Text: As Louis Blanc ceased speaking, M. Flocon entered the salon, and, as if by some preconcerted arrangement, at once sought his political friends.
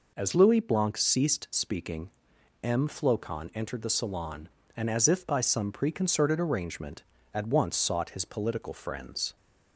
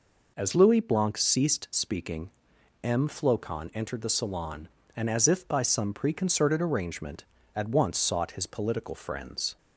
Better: neither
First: none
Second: none

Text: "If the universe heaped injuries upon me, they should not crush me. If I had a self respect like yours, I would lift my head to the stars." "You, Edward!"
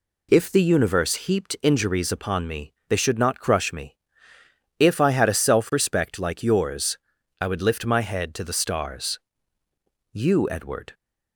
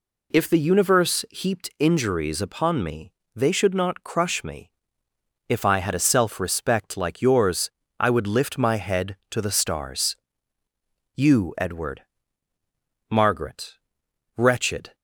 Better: first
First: none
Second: goes on to say "Margaret wretched"; strong; from 13.1 s on; 1.8 s long

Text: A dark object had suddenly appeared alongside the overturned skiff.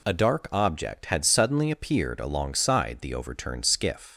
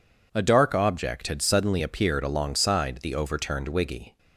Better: first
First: none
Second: says "wiggy" for "skiff"; at 3.6 s

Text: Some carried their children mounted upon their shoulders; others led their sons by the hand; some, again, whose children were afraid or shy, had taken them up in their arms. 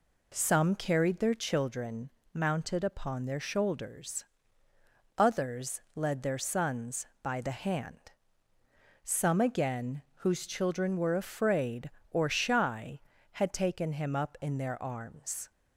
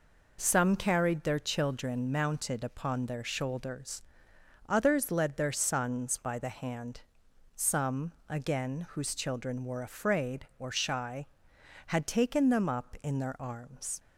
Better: second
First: pauses between "children" and "mounted"; slight; at 2.0 s; 0.24 s long // says "him" for "them"; at 13.9 s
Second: none

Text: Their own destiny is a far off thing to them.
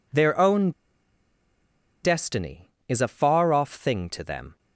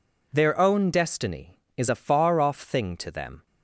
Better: second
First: pauses between "own" and "destiny"; strong; at 0.7 s; 1.3 s long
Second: none

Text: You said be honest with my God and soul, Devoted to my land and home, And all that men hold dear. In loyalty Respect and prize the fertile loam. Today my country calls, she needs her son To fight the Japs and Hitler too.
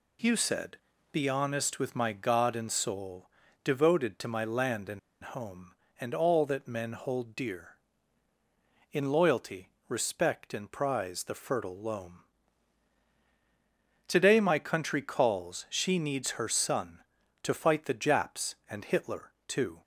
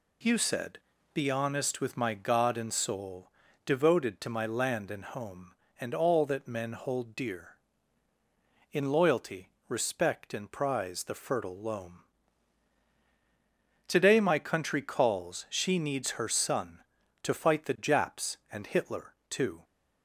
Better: second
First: pauses between "said" and "be"; slight; at 0.7 s; 0.36 s long // pauses between "and" and "home"; slight; at 4.9 s; 0.24 s long // pauses between "loyalty" and "Respect"; slight; at 9.6 s; 0.20 s long // pauses between "Hitler" and "too"; slight; at 19.2 s; 0.16 s long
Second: pauses between "said" and "be"; slight; at 0.7 s; 0.36 s long // pauses between "loyalty" and "Respect"; slight; at 9.4 s; 0.20 s long // pauses between "Hitler" and "too"; slight; at 19.1 s; 0.16 s long

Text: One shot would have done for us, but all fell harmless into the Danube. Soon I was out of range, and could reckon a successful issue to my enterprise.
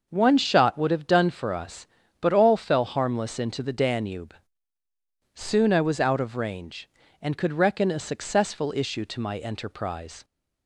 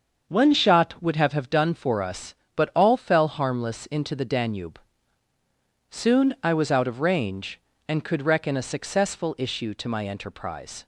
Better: first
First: none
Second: starts louder than the rest; until 1.2 s; 6.5 dB // says "have" twice; at 1.3 s

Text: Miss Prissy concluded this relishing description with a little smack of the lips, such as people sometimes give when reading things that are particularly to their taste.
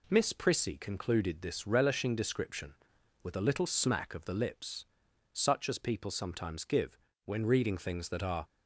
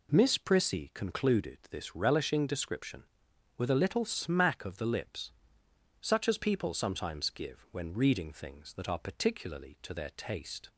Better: second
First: pauses between "give" and "when"; slight; at 6.9 s; 0.26 s long // stops before "particularly to their taste"; at 8.4 s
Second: none

